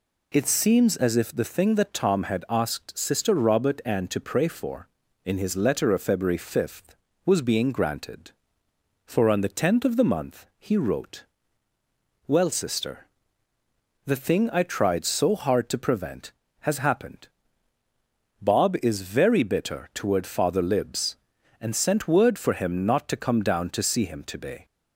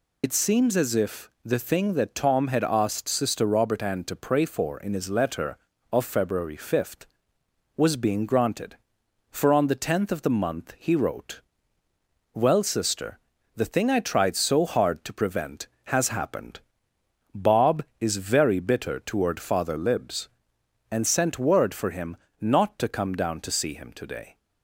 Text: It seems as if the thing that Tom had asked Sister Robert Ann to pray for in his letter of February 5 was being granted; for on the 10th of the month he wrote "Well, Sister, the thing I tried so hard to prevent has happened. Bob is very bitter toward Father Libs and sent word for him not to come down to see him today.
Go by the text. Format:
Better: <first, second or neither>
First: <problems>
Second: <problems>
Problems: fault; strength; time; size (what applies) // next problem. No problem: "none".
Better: first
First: pauses between "wrote" and "Well"; at 11.2 s; 1.0 s long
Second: loses the start of "It"; at 0.2 s; 60 ms // pauses between "if" and "the"; slight; at 1.2 s; 0.16 s long // pauses between "wrote" and "Well"; noticeable; at 11.4 s; 0.92 s long // pauses between "him" and "not"; slight; at 22.1 s; 0.26 s long